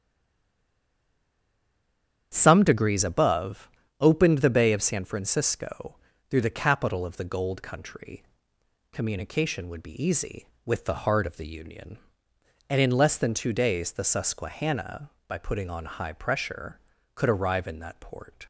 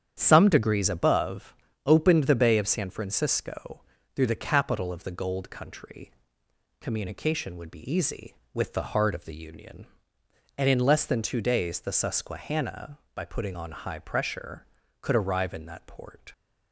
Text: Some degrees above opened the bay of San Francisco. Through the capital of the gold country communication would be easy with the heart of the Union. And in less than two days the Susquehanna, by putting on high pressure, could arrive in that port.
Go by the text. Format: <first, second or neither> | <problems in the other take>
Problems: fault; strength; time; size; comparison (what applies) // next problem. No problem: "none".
second | stays silent before the first word; until 2.3 s; 2.3 s long // starts louder than the rest; strong; until 3.3 s; 9 dB; strong in the second // pauses between "above" and "opened"; slight; at 3.6 s; 0.32 s long; slight in the second // pauses between "country" and "communication"; noticeable; at 8.2 s; 0.70 s long; noticeable in the second